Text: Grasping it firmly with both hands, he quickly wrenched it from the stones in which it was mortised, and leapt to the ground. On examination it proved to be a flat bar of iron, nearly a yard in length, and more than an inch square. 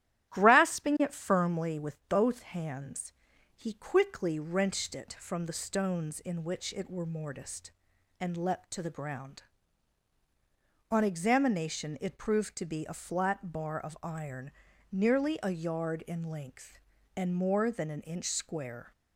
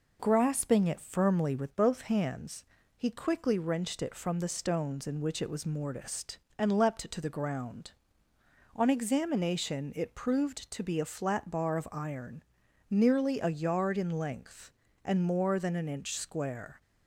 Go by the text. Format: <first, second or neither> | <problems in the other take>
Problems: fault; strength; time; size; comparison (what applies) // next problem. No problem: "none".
second | starts louder than the rest; strong; until 1.3 s; 12.5 dB // says "were" for "was"; at 6.8 s